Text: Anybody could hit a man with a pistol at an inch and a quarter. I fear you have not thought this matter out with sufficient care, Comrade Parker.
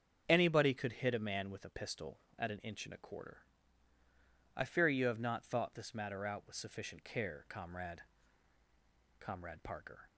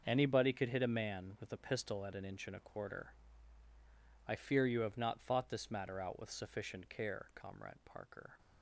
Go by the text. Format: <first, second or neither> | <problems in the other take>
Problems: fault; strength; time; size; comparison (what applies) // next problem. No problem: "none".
second | starts louder than the rest; strong; until 1.2 s; 7.5 dB; also in the second // says "Comrade" twice; at 9.1 s